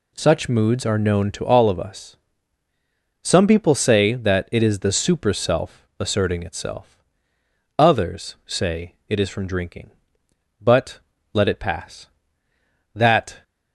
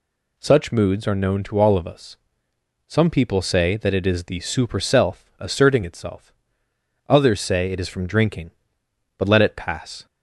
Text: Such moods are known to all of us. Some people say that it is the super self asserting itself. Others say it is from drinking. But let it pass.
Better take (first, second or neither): second